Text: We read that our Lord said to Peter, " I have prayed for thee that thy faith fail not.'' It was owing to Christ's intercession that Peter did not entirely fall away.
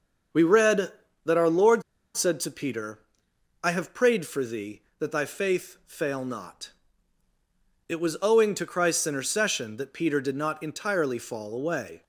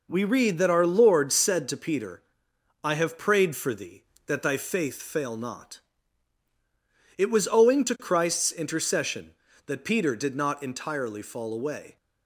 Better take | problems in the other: second | starts louder than the rest; until 1.6 s; 6.5 dB // pauses between "Lord" and "said"; slight; at 1.8 s; 0.32 s long

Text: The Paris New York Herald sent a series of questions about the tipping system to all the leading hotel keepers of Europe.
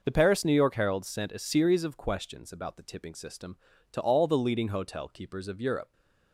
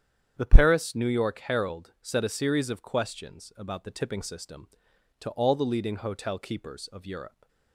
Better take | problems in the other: first | starts louder than the rest; strong; until 1.3 s; 7.5 dB // says "set" for "sent"; at 1.9 s

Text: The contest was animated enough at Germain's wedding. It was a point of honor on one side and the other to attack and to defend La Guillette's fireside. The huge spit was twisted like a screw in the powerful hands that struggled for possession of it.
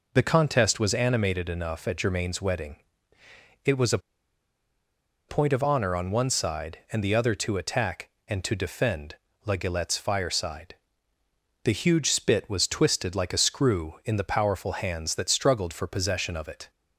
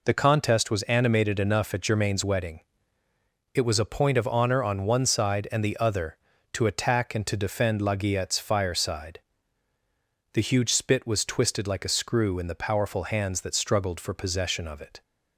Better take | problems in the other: second | pauses between "a" and "point"; strong; at 3.9 s; 1.3 s long // pauses between "defend" and "La"; slight; at 9.1 s; 0.32 s long

